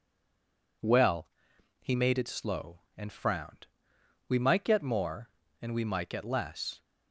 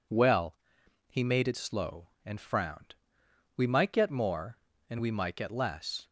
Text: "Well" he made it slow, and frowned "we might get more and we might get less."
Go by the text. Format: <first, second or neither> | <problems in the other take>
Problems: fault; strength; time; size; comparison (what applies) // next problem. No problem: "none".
second | stays silent before the first word; slight; until 0.8 s; 0.8 s long // pauses between "Well" and "he"; noticeable; at 1.2 s; 0.54 s long; noticeable in the second // pauses between "frowned" and "we"; noticeable; at 3.6 s; 0.62 s long; noticeable in the second